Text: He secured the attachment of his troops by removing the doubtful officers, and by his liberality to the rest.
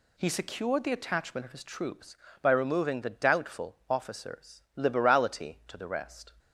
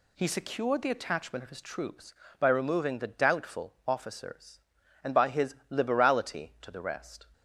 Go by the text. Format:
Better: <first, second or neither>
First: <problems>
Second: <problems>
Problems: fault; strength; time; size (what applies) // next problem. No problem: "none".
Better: second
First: skips "and by his"; at 4.6 s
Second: none